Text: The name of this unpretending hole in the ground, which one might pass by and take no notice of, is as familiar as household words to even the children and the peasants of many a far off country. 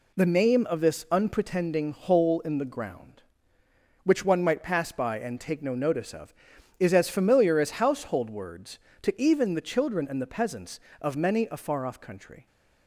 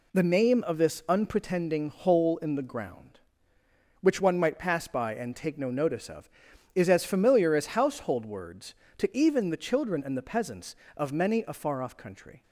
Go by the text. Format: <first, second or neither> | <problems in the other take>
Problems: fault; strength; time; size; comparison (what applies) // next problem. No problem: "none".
neither | none